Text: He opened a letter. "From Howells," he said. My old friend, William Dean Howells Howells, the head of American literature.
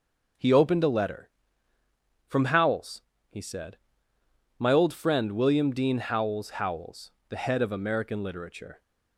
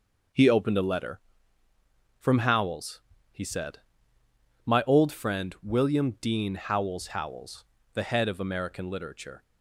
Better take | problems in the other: neither | none

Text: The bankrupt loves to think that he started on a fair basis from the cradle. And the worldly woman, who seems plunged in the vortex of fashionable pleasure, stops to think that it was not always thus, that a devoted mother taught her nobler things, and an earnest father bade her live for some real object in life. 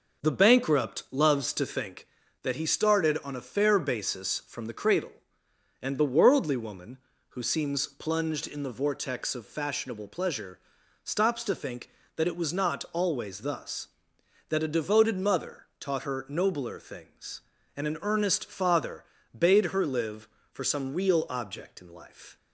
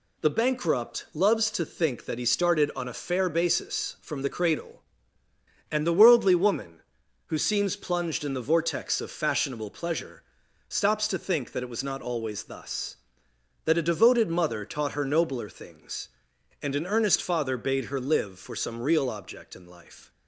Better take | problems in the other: second | starts louder than the rest; noticeable; until 1.9 s; 5.5 dB // pauses between "mother" and "taught"; slight; at 15.6 s; 0.16 s long // pauses between "father" and "bade"; slight; at 19.0 s; 0.32 s long

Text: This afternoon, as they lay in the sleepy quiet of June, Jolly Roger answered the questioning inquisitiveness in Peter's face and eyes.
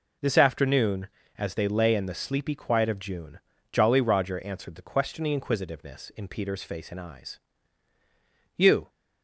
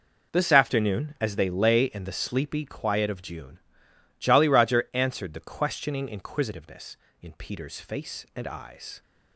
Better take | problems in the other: second | goes on to say "You"; slight; from 8.5 s on; 0.32 s long

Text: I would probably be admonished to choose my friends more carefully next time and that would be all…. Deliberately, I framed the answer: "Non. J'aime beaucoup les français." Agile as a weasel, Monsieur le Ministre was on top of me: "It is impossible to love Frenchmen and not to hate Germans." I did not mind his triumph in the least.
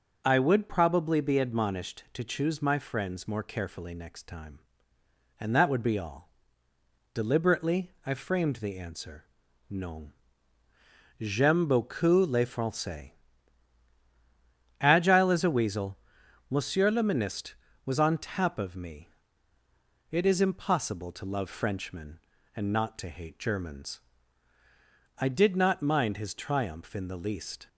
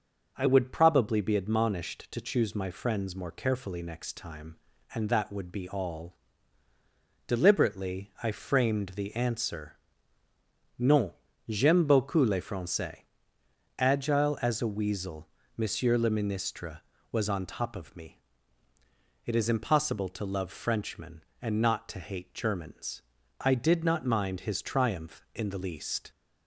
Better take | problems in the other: second | says "tap" for "top"; at 18.1 s

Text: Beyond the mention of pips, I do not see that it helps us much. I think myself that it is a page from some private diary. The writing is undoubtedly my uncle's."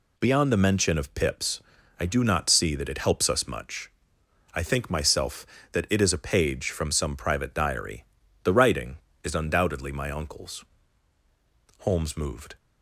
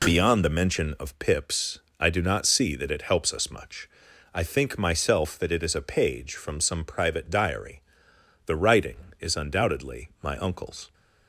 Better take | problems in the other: second | goes on to say "Holmes moved"; noticeable; from 11.8 s on; 0.76 s long

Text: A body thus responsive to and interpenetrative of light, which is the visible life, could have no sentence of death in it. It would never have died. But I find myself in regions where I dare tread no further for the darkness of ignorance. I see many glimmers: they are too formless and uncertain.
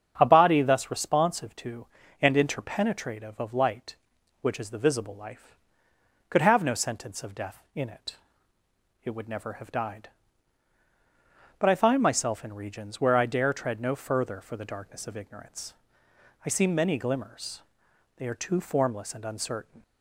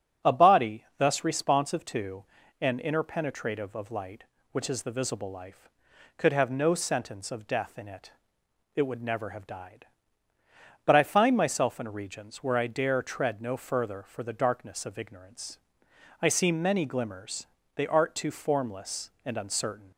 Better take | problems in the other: first | starts louder than the rest; strong; until 1.3 s; 8 dB; strong in the first // says "art" for "are"; at 17.8 s

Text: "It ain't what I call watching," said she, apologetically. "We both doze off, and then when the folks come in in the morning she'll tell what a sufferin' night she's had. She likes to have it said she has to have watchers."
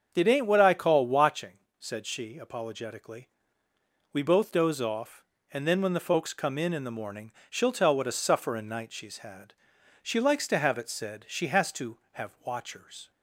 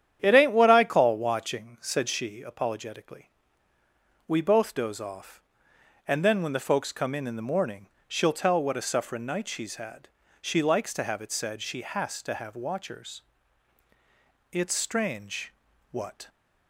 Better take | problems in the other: first | starts louder than the rest; strong; until 1.2 s; 9.5 dB; also in the first // pauses between "morning" and "she'll"; slight; at 7.8 s; 0.18 s long; slight in the first // goes on to say "It's strange what"; strong; from 14.5 s on; 1.7 s long

